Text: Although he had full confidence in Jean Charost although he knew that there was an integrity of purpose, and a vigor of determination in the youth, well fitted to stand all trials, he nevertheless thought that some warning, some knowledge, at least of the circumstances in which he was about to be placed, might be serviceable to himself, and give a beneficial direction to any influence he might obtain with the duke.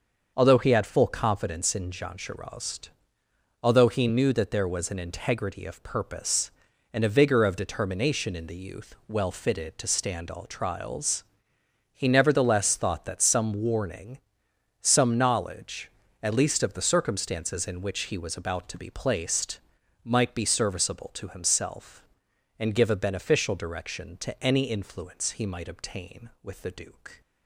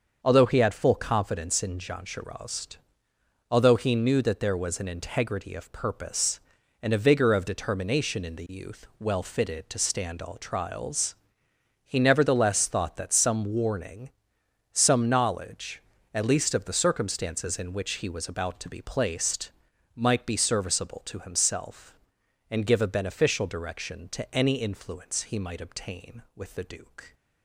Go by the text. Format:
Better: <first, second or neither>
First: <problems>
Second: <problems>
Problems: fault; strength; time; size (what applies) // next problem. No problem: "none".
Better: neither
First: starts louder than the rest; until 1.3 s; 6.5 dB // pauses between "Charost" and "although"; noticeable; at 2.8 s; 0.74 s long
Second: starts louder than the rest; until 1.2 s; 6.5 dB // pauses between "Charost" and "although"; noticeable; at 2.7 s; 0.74 s long